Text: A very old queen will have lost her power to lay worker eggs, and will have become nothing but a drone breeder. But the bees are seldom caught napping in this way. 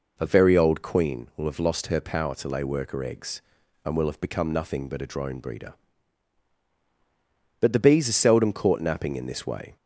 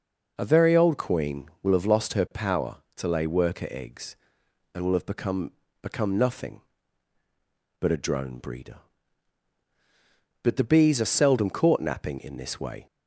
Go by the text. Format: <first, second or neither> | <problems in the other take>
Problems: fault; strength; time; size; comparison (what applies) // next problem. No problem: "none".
first | says "become" twice; at 5.7 s